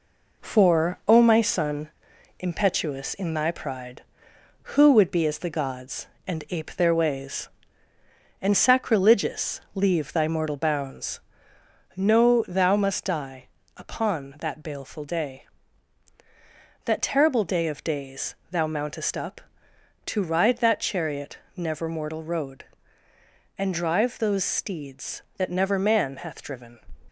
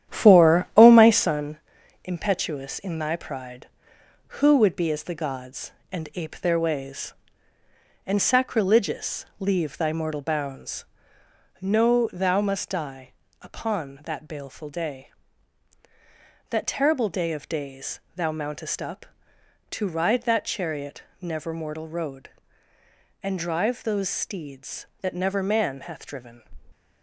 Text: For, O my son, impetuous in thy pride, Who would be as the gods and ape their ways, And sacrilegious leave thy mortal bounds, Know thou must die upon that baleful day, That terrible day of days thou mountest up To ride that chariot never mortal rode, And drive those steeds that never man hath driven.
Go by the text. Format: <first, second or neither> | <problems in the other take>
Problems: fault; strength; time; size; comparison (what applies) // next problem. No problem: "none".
first | starts louder than the rest; strong; until 1.5 s; 10.5 dB // pauses between "die" and "upon"; slight; at 13.1 s; 0.30 s long; slight in the first // pauses between "days" and "thou"; slight; at 17.9 s; 0.16 s long; slight in the first // pauses between "chariot" and "never"; slight; at 21.0 s; 0.18 s long; slight in the first